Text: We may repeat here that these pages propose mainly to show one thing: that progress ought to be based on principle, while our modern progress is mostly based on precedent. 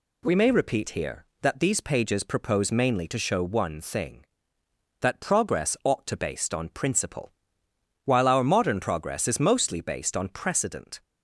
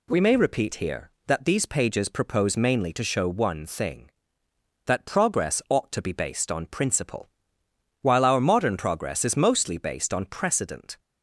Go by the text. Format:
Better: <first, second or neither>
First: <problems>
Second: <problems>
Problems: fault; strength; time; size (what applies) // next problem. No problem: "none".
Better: second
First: skips "be"; at 6.1 s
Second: none